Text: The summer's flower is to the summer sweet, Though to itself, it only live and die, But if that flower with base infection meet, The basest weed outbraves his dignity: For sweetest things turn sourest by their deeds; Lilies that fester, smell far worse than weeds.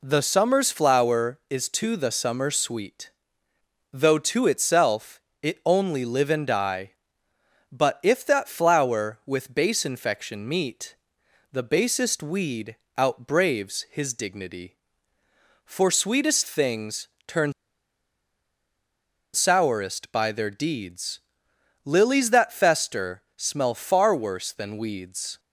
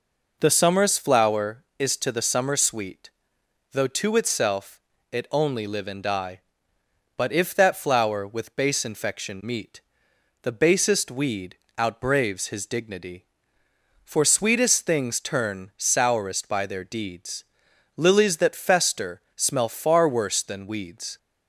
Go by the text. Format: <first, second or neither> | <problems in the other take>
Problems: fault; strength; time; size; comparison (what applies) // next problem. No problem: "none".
second | pauses between "weed" and "outbraves"; slight; at 12.7 s; 0.20 s long; slight in the second // pauses between "things" and "turn"; slight; at 17.0 s; 0.18 s long // pauses between "turn" and "sourest"; strong; at 17.5 s; 1.8 s long